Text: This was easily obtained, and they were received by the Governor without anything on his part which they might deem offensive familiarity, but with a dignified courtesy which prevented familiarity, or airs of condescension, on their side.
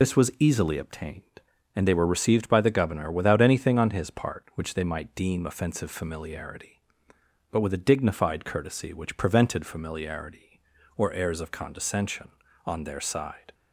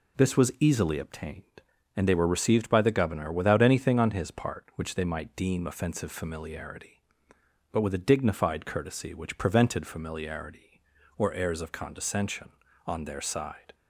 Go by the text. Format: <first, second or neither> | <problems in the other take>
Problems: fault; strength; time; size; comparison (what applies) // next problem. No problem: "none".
second | loses the start of "This"; at 0.0 s; 50 ms